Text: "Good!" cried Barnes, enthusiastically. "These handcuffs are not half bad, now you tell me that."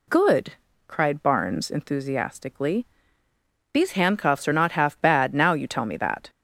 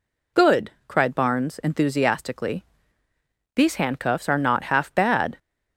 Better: first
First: none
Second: stops before "now you tell me that"; at 5.3 s

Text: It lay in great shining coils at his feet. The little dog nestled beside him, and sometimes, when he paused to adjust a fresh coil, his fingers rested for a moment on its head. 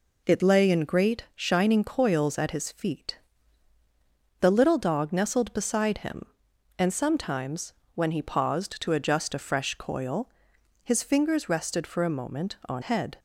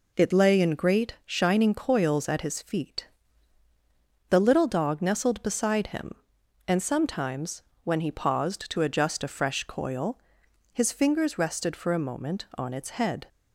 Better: second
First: skips "its"; at 12.8 s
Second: none

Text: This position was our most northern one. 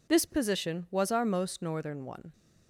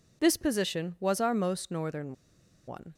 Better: first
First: none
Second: pauses between "northern" and "one"; noticeable; at 2.1 s; 0.54 s long

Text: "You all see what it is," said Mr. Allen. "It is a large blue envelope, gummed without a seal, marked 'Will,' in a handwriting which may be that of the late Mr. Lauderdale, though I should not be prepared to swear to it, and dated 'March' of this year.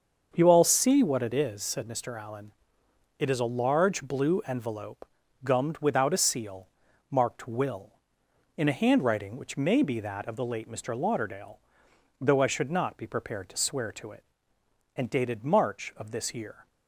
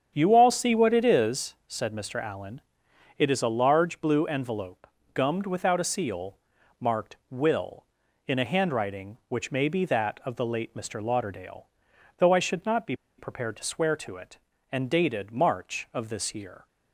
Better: first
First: starts louder than the rest; until 1.3 s; 6.5 dB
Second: starts louder than the rest; strong; until 1.1 s; 8 dB // pauses between "be" and "prepared"; slight; at 12.9 s; 0.23 s long

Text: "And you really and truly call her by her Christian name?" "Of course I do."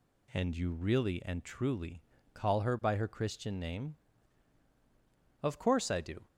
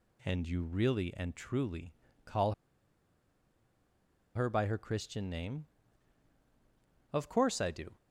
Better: first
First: pauses between "truly" and "call"; slight; at 2.0 s; 0.32 s long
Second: pauses between "truly" and "call"; slight; at 1.9 s; 0.32 s long // pauses between "call" and "her"; strong; at 2.5 s; 1.8 s long

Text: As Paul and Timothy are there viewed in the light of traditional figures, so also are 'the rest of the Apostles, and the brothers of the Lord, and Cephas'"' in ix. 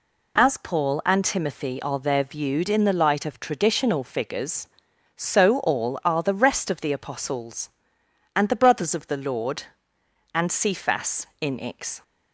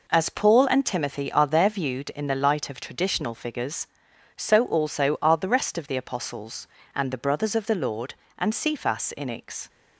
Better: second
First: says "all" for "also"; at 5.6 s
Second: none

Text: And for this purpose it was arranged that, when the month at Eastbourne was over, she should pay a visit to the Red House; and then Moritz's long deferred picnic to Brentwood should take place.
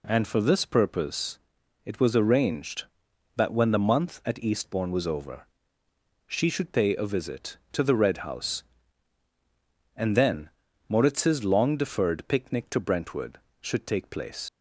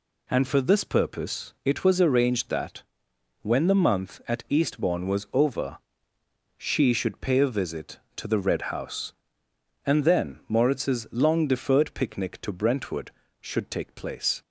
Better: second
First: pauses between "purpose" and "it"; at 1.3 s; 0.44 s long // pauses between "then" and "Moritz's"; at 10.4 s; 0.38 s long // leaves "place" unfinished; at 14.4 s; 50 ms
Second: none

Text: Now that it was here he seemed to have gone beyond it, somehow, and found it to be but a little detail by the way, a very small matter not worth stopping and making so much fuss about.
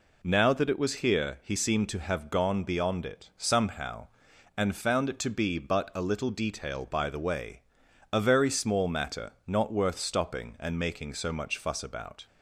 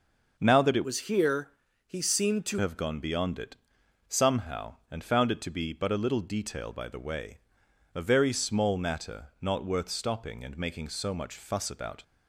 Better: first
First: none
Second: starts louder than the rest; noticeable; until 1.3 s; 6 dB // changes voice from "was" to "to"; from 0.8 to 2.5 s; 1.7 s long // pauses between "here" and "he"; slight; at 1.5 s; 0.36 s long

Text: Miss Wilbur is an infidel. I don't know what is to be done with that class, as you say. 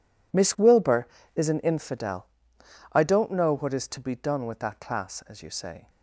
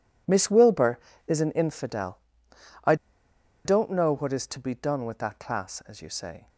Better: first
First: none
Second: pauses between "I" and "don't"; noticeable; at 2.9 s; 0.70 s long

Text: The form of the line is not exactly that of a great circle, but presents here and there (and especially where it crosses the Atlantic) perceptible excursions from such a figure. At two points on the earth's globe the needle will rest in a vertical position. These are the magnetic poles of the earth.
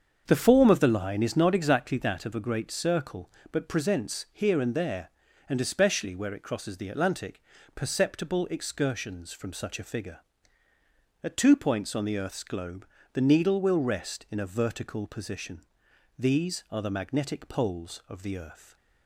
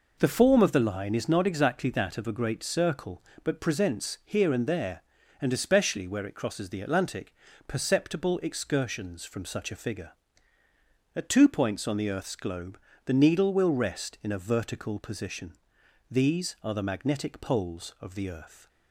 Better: second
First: starts louder than the rest; until 2.0 s; 7 dB // pauses between "globe" and "the"; slight; at 12.8 s; 0.26 s long // stays silent after the last word; slight; from 18.5 s on; 0.5 s long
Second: pauses between "globe" and "the"; slight; at 12.7 s; 0.26 s long

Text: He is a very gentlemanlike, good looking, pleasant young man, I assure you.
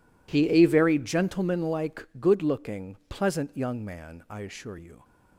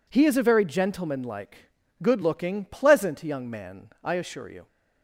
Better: second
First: skips "is"; at 0.4 s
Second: none

